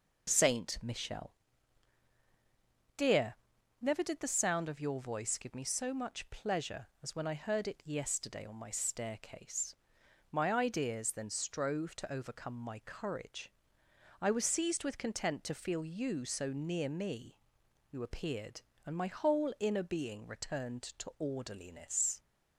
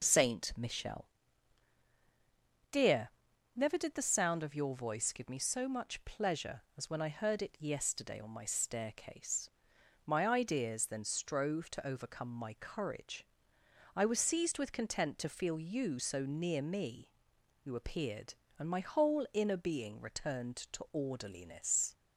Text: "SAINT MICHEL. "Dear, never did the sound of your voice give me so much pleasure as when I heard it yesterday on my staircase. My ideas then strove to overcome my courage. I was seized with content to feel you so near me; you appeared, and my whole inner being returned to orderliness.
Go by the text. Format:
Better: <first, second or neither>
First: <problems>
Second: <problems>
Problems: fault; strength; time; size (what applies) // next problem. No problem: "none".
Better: neither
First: none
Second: none